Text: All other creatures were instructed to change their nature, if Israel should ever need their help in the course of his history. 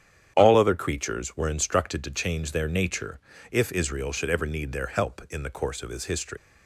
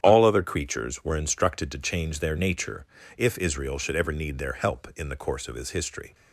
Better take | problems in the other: second | starts louder than the rest; strong; until 1.3 s; 9 dB; strong in the second // leaves "history" unfinished; at 6.3 s; 115 ms

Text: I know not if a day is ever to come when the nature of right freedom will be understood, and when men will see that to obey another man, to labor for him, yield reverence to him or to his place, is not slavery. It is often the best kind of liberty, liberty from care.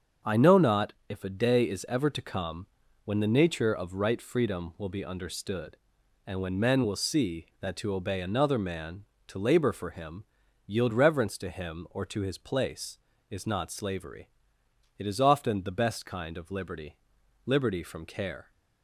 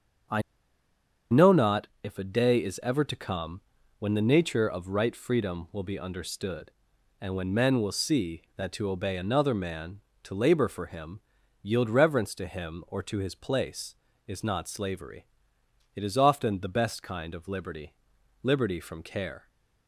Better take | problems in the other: first | starts louder than the rest; until 2.4 s; 7 dB; also in the first // pauses between "I" and "know"; noticeable; at 0.4 s; 0.90 s long // pauses between "not" and "if"; slight; at 1.8 s; 0.16 s long; slight in the first // pauses between "come" and "when"; at 3.6 s; 0.38 s long; also in the first

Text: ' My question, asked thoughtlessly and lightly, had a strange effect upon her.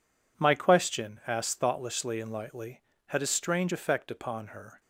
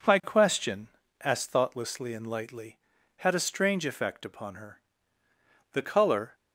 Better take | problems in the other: first | goes on to say "The colour"; noticeable; from 5.7 s on; 0.62 s long

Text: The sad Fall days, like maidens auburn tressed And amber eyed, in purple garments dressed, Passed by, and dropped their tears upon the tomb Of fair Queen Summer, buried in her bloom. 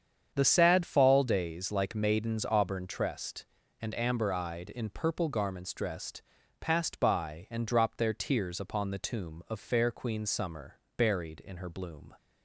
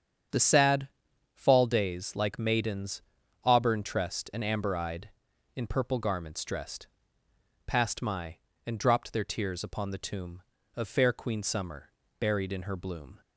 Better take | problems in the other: first | starts louder than the rest; strong; until 1.7 s; 7.5 dB; strong in the first // pauses between "sad" and "Fall"; noticeable; at 0.8 s; 0.46 s long // pauses between "maidens" and "auburn"; at 3.0 s; 0.40 s long // says "my" for "by"; at 8.0 s

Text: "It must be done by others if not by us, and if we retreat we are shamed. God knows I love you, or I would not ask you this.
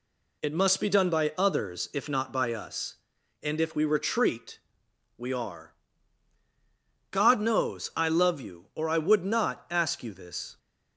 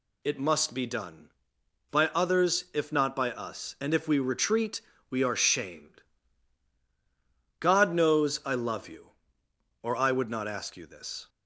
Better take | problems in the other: second | pauses between "retreat" and "we"; noticeable; at 4.5 s; 0.58 s long; slight in the second // skips "shamed"; at 6.4 s

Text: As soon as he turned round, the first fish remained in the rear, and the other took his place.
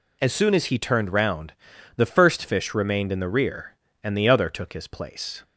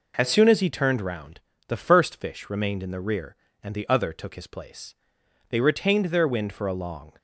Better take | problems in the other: first | goes on to say "They retained their wind for a long"; strong; from 5.4 s on; 1.6 s long

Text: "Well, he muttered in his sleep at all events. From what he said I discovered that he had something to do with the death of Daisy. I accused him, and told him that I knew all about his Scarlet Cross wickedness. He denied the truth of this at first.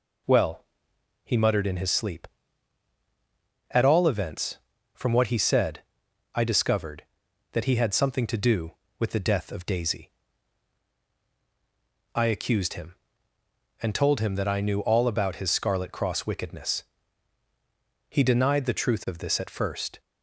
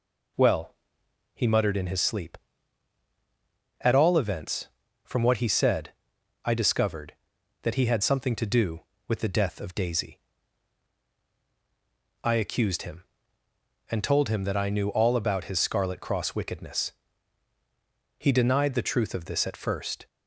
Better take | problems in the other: neither | pauses between "said" and "I"; noticeable; the same in both

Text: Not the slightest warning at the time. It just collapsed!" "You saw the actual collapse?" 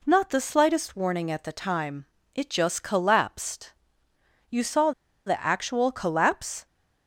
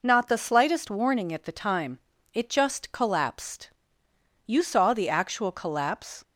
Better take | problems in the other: second | pauses between "saw" and "the"; slight; at 4.9 s; 0.35 s long

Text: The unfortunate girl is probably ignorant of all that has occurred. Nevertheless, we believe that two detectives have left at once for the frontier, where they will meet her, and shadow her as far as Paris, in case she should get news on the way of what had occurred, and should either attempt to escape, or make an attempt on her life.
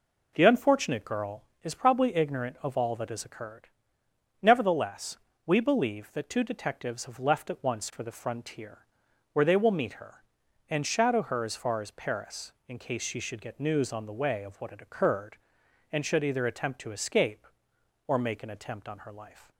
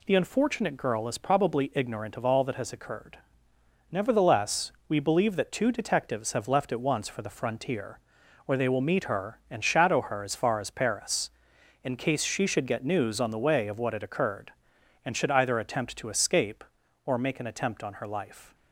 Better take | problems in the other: neither | none

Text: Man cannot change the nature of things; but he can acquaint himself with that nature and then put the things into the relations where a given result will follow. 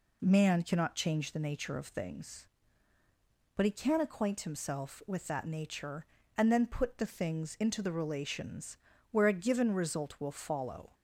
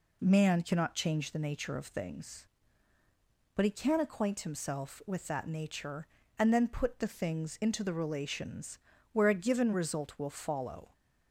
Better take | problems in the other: neither | pauses between "relations" and "where"; slight; the same in both

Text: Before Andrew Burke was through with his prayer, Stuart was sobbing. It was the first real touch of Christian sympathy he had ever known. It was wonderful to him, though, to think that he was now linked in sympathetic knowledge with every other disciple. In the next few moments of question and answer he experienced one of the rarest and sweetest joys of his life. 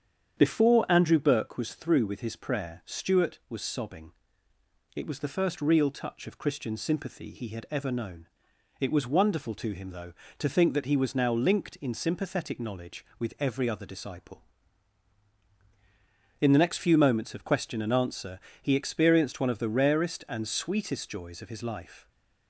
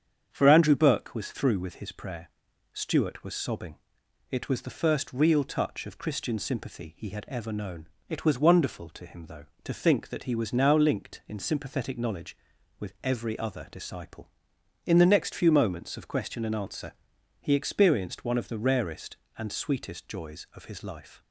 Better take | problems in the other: first | starts louder than the rest; strong; until 1.3 s; 8 dB; strong in the first // says "For" for "Before"; at 0.3 s // pauses between "answer" and "he"; noticeable; at 16.9 s; 0.50 s long; slight in the first

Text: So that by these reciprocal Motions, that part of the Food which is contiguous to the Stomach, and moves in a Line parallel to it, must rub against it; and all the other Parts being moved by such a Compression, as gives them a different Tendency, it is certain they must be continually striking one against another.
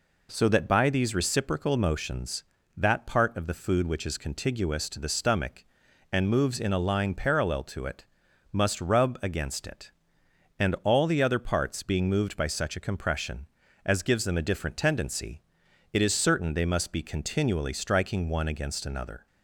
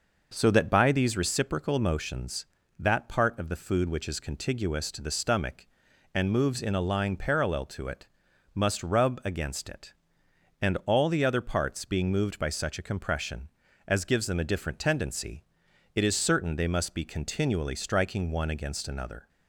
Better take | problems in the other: first | starts louder than the rest; noticeable; until 1.2 s; 5.5 dB

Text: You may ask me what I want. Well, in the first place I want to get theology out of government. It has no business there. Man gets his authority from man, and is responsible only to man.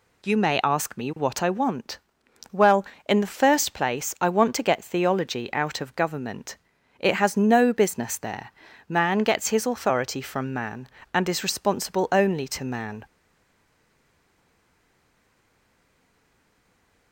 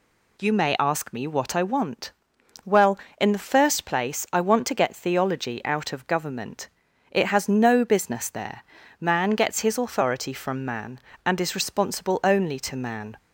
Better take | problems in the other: second | stays silent after the last word; strong; from 13.0 s on; 4.1 s long

